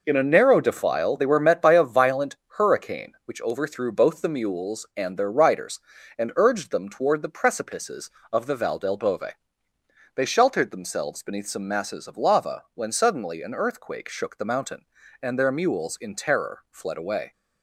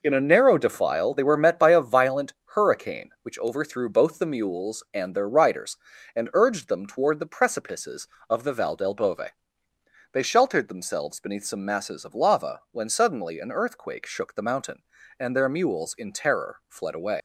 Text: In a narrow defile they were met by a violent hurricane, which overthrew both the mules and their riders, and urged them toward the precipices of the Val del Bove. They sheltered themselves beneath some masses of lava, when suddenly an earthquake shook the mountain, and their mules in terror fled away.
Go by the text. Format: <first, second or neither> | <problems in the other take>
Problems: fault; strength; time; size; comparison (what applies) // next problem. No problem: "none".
first | pauses between "violent" and "hurricane"; slight; at 2.3 s; 0.22 s long; slight in the first // leaves "away" unfinished; at 17.1 s; 90 ms